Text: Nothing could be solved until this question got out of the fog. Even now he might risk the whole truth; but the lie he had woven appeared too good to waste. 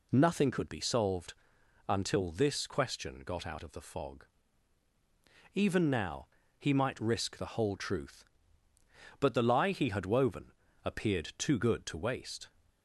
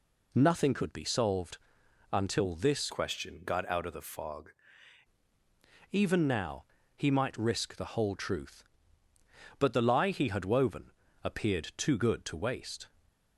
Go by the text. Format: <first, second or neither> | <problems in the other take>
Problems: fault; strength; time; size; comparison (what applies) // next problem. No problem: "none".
first | pauses between "solved" and "until"; noticeable; at 1.5 s; 0.54 s long; noticeable in the first // changes voice from "question" to "fog"; from 2.9 to 4.4 s; 1.5 s long // pauses between "now" and "he"; slight; at 6.6 s; 0.32 s long; slight in the first // pauses between "woven" and "appeared"; slight; at 10.9 s; 0.32 s long; slight in the first